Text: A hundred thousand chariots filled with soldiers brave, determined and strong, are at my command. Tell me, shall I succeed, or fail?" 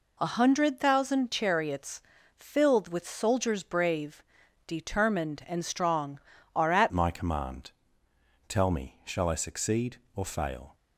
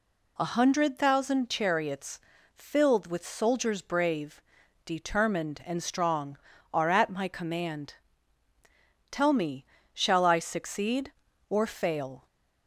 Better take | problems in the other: second | pauses between "chariots" and "filled"; slight; at 2.0 s; 0.34 s long; slight in the second // changes voice at "my"; from 6.9 s on; 3.8 s long

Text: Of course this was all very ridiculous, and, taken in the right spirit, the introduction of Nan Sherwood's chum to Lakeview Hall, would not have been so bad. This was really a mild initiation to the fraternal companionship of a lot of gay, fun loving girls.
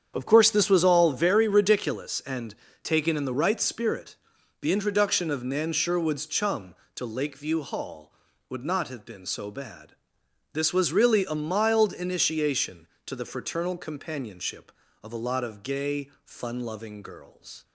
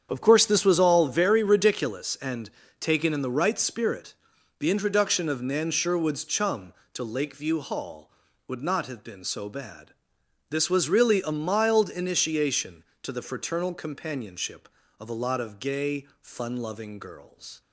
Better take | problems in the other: neither | starts louder than the rest; strong; the same in both

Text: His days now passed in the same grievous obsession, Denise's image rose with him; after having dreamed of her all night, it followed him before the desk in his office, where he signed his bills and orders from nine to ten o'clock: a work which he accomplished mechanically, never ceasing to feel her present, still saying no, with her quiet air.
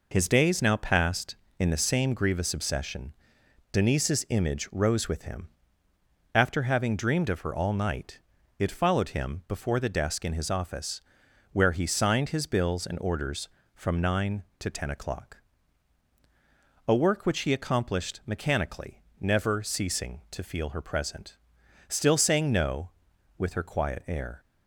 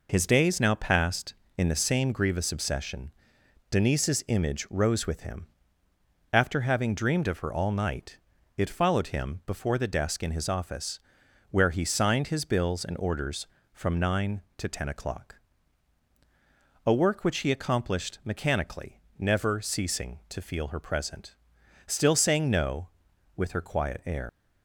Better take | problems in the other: first | leaves "air" unfinished; at 24.2 s; 90 ms

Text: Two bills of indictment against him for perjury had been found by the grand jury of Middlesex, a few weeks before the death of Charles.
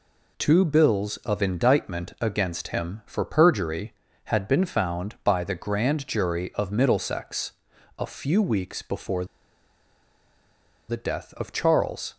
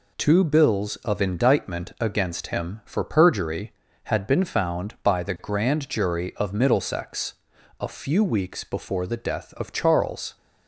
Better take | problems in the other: second | pauses between "before" and "the"; strong; at 9.2 s; 1.6 s long

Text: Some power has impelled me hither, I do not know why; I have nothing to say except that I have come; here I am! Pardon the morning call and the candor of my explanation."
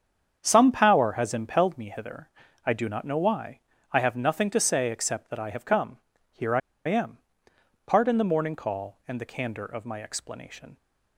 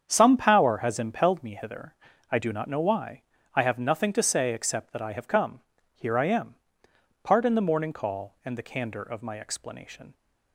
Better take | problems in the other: second | starts louder than the rest; strong; until 1.4 s; 7.5 dB; strong in the second // pauses between "I" and "am"; slight; at 6.6 s; 0.26 s long

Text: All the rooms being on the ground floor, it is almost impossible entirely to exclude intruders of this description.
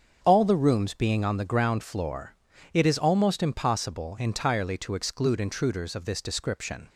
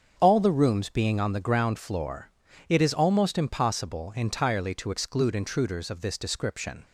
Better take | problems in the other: neither | starts louder than the rest; the same in both

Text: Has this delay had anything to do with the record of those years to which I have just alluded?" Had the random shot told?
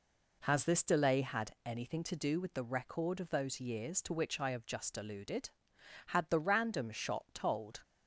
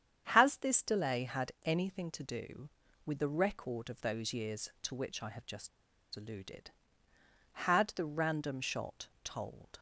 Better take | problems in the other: first | starts louder than the rest; strong; until 1.3 s; 8.5 dB // pauses between "just" and "alluded"; at 5.6 s; 0.45 s long // pauses between "shot" and "told"; slight; at 9.0 s; 0.16 s long

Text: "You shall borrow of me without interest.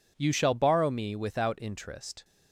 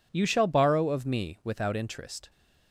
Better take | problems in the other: second | skips "of"; at 0.9 s

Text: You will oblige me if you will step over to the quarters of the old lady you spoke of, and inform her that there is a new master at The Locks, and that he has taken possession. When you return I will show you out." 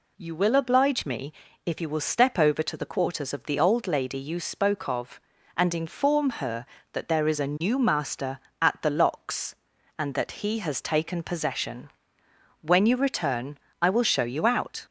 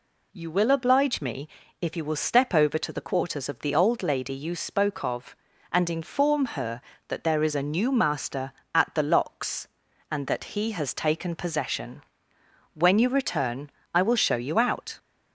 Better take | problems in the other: neither | pauses between "me" and "if"; slight; the same in both // pauses between "return" and "I"; slight; the same in both

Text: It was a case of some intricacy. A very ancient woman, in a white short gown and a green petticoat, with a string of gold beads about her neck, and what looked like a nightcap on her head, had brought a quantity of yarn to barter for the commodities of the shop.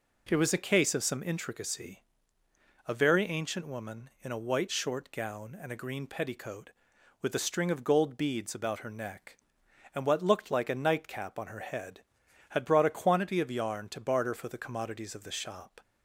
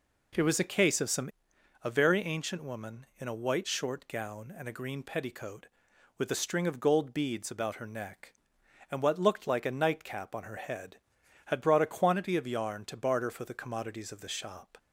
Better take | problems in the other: first | skips "intricacy"; at 1.5 s

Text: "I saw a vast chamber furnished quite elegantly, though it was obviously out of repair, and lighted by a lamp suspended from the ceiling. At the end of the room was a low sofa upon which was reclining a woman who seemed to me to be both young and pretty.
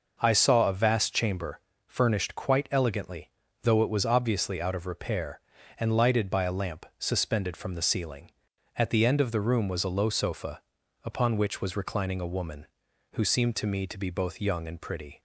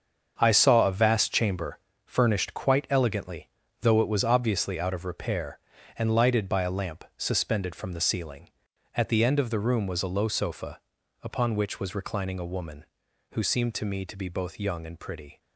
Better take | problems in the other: first | gets quieter; strong; throughout; 9.5 dB // pauses between "chamber" and "furnished"; slight; at 1.7 s; 0.26 s long; slight in the first // pauses between "sofa" and "upon"; at 10.7 s; 0.42 s long; also in the first

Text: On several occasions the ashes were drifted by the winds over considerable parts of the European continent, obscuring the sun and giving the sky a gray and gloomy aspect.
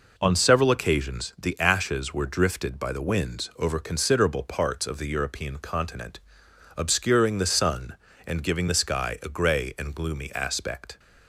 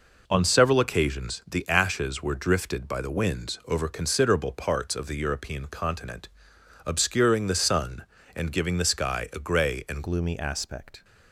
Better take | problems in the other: first | changes voice at "gloomy"; from 10.0 s on; 1.0 s long

